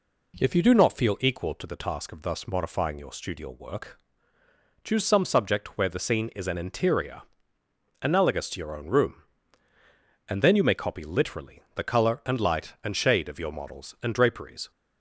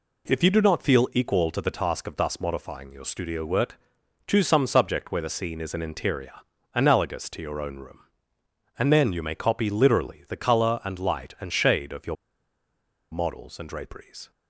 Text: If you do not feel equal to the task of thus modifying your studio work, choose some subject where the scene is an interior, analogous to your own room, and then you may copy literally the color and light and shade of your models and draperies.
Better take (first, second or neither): first